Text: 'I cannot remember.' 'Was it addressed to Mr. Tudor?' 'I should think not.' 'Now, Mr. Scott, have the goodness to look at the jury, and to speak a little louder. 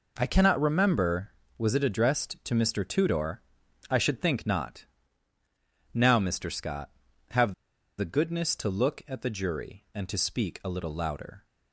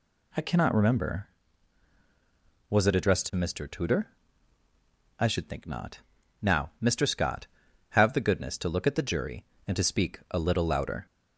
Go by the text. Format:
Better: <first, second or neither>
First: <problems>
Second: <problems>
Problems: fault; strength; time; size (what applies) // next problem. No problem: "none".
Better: second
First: pauses between "have" and "the"; at 7.5 s; 0.45 s long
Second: none